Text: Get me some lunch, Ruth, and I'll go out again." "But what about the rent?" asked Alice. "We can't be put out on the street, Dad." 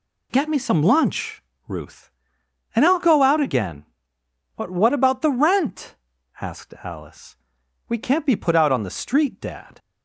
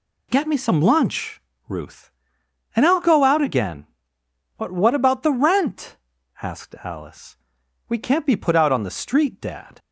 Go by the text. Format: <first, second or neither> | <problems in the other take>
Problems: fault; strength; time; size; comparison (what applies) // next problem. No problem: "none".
neither | none